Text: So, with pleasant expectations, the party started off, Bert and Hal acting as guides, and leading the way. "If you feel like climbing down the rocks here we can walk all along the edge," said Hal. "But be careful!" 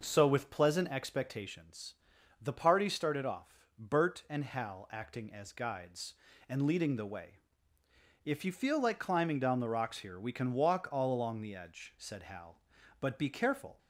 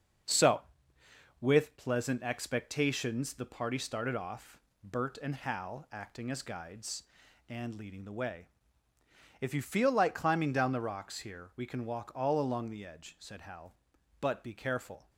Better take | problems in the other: first | gets quieter; noticeable; throughout; 5.5 dB

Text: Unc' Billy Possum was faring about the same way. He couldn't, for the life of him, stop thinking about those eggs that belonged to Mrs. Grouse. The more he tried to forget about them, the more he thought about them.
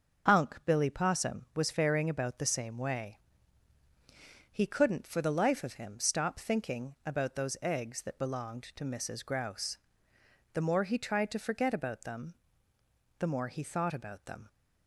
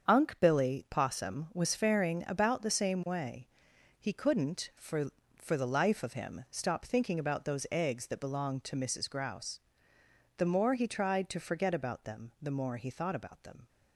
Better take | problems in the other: first | starts louder than the rest; strong; until 1.1 s; 7 dB // says "for" twice; at 5.3 s

